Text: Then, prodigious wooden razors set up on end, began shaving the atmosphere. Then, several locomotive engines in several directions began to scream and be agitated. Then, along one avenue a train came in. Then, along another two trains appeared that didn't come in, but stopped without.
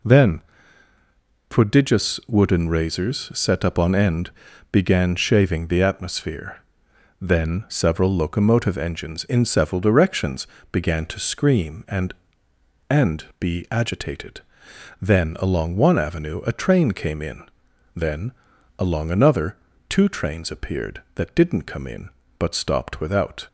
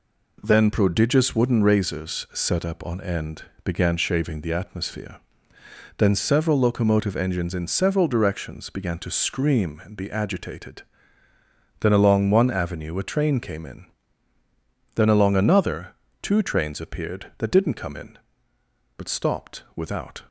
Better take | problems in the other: second | pauses between "directions" and "began"; slight; at 10.4 s; 0.26 s long // says "and" twice; at 12.8 s // pauses between "another" and "two"; slight; at 19.5 s; 0.32 s long; slight in the second

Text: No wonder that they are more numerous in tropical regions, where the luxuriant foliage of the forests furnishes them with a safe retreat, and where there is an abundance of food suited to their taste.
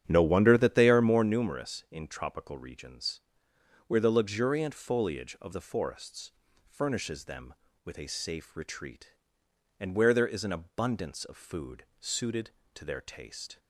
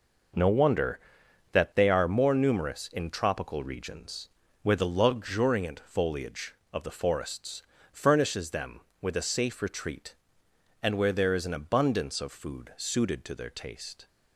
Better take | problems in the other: second | starts louder than the rest; strong; until 1.3 s; 9.5 dB // pauses between "forests" and "furnishes"; slight; at 6.3 s; 0.34 s long; slight in the second // pauses between "food" and "suited"; slight; at 11.8 s; 0.16 s long

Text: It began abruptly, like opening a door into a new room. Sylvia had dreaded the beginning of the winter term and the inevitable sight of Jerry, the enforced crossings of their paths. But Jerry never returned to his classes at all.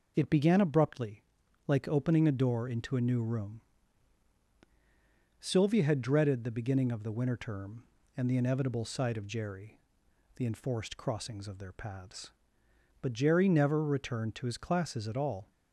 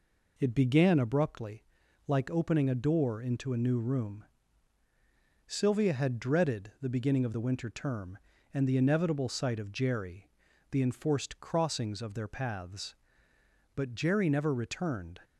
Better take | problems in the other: first | stops before "to his classes at all"; at 15.2 s

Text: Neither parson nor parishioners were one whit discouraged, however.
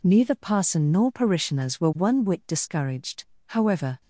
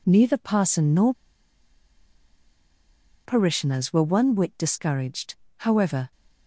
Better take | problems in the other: first | pauses between "nor" and "parishioners"; strong; at 1.1 s; 2.1 s long

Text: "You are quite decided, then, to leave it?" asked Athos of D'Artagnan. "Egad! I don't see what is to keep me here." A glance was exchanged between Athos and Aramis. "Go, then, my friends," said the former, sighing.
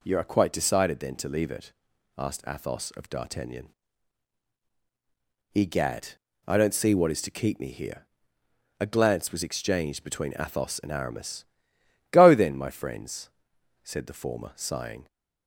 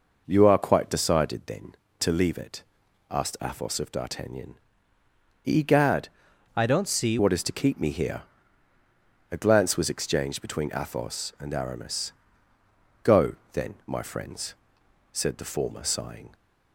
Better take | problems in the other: first | changes voice from "I" to "see"; from 6.5 to 7.1 s; 0.6 s long

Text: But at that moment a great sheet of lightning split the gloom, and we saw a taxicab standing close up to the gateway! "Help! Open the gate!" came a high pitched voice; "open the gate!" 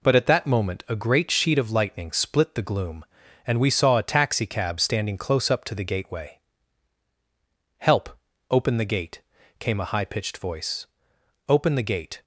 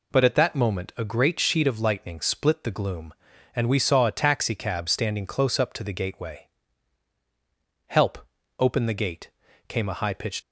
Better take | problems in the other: first | stops before "voice open the gate"; at 10.4 s

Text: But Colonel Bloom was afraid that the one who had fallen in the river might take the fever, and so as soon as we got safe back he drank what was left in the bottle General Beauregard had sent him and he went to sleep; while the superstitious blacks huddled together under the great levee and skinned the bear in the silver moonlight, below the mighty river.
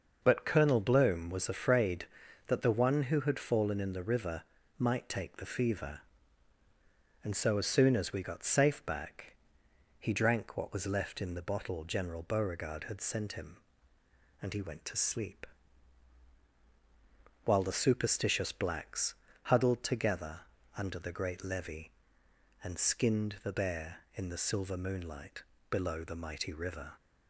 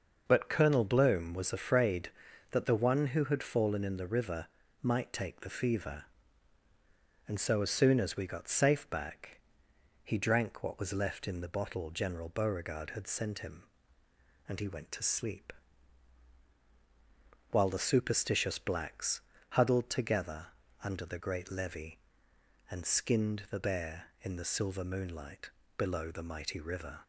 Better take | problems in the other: neither | starts louder than the rest; noticeable; the same in both // pauses between "river" and "might"; slight; the same in both // pauses between "back" and "he"; noticeable; the same in both // pauses between "blacks" and "huddled"; slight; the same in both // pauses between "together" and "under"; slight; the same in both

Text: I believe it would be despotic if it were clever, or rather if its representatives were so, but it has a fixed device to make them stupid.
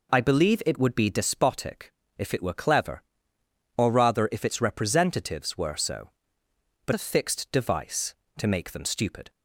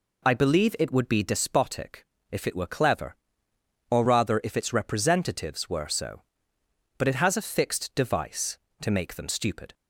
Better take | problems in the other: second | pauses between "despotic" and "if"; slight; at 1.9 s; 0.26 s long; slight in the second // skips "it has"; at 6.9 s

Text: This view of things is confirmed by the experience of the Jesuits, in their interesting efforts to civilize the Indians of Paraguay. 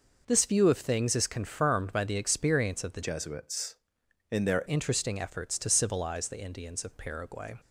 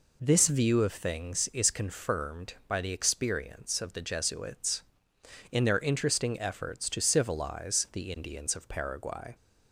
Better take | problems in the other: second | changes voice from "Jesuits" to "their"; from 3.0 to 4.6 s; 1.6 s long

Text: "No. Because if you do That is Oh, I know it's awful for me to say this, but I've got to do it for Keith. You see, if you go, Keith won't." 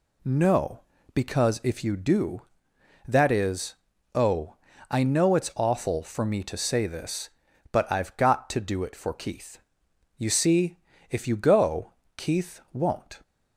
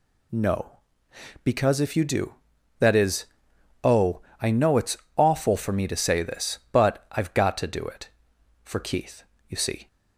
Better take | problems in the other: first | pauses between "is" and "Oh"; noticeable; at 3.2 s; 0.58 s long; also in the first // pauses between "it's" and "awful"; slight; at 4.9 s; 0.18 s long // stops before "if you go Keith won't"; at 9.8 s

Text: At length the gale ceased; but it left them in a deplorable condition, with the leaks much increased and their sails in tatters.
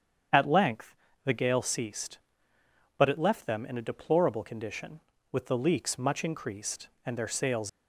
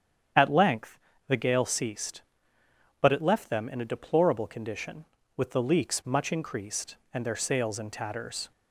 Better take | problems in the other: second | starts louder than the rest; strong; until 1.6 s; 8 dB; strong in the second // pauses between "length" and "the"; slight; at 0.9 s; 0.28 s long; slight in the second // stops before "in tatters"; at 7.6 s

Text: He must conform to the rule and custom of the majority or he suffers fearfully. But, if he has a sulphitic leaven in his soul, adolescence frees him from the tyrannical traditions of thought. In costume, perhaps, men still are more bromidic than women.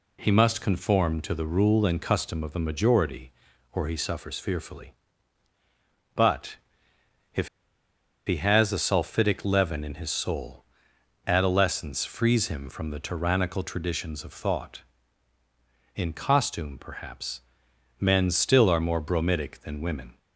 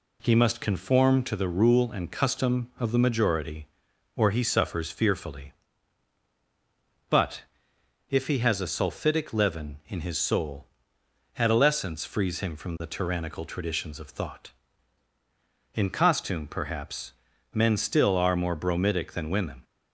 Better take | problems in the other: second | pauses between "if" and "he"; noticeable; at 7.4 s; 0.79 s long

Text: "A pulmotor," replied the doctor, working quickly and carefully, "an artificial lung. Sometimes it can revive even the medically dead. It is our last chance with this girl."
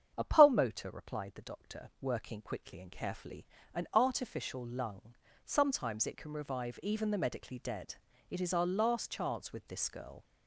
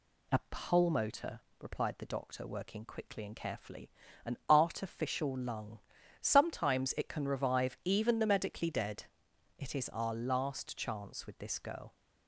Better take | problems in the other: second | gets louder; throughout; 3.5 dB // starts louder than the rest; strong; until 1.1 s; 8 dB

